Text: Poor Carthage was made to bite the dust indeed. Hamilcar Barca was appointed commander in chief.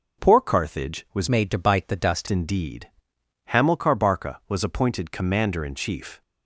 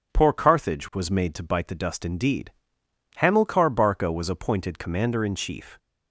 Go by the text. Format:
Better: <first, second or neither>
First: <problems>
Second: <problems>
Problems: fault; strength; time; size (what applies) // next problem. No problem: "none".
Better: second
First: changes voice from "made" to "dust"; from 1.2 to 2.2 s; 1.0 s long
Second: none